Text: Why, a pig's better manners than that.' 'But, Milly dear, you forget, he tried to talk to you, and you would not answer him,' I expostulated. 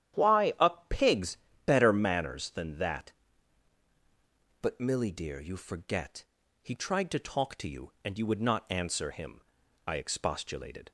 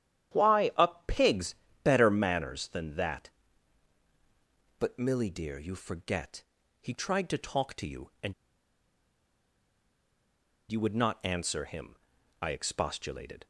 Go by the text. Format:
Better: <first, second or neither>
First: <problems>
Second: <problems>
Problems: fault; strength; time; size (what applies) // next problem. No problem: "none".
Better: first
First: starts louder than the rest; strong; until 1.7 s; 10.5 dB // pauses between "a" and "pig's"; slight; at 0.7 s; 0.18 s long // pauses between "pig's" and "better"; slight; at 1.3 s; 0.30 s long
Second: starts louder than the rest; strong; until 1.8 s; 10.5 dB // pauses between "a" and "pig's"; slight; at 0.8 s; 0.18 s long // pauses between "pig's" and "better"; slight; at 1.5 s; 0.30 s long // pauses between "and" and "you"; strong; at 8.3 s; 2.3 s long